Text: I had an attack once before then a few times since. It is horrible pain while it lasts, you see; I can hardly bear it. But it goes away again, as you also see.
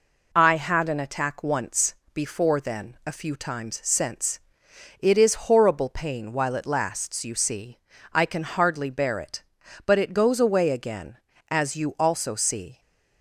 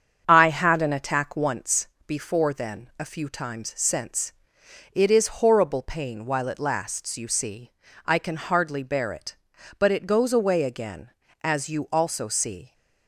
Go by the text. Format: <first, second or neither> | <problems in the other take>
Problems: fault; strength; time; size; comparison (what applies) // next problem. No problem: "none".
first | starts louder than the rest; strong; until 1.5 s; 7.5 dB // pauses between "once" and "before"; slight; at 1.8 s; 0.20 s long; slight in the first